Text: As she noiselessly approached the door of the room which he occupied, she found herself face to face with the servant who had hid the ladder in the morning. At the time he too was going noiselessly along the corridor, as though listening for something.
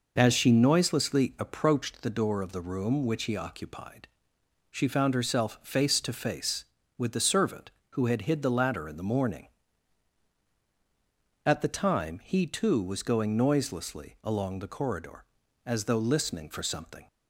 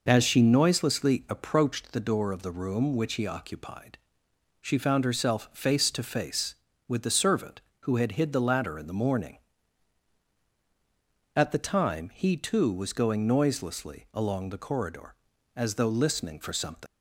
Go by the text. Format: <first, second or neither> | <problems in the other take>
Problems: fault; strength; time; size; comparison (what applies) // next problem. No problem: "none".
first | leaves "something" unfinished; at 16.8 s; 105 ms